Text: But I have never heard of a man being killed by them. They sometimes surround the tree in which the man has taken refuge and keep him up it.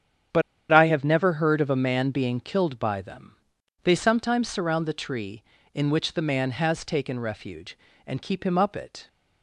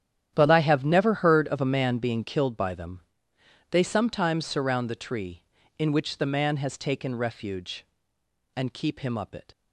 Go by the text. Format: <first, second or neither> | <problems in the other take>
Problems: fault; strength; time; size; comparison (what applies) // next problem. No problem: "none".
second | starts louder than the rest; strong; until 1.6 s; 9 dB; strong in the second // pauses between "But" and "I"; slight; at 0.4 s; 0.29 s long